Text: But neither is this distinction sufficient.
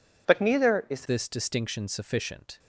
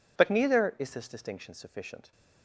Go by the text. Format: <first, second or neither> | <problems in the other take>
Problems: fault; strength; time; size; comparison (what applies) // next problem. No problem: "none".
second | changes voice at "this"; from 1.0 s on; 1.5 s long